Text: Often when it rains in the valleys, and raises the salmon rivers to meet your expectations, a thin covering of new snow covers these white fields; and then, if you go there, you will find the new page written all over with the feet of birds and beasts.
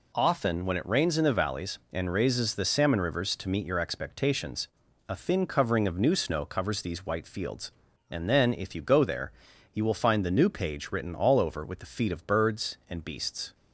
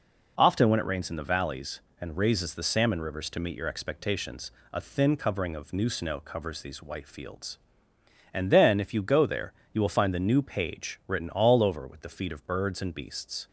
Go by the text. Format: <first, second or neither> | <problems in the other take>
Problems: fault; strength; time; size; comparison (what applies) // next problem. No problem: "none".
neither | none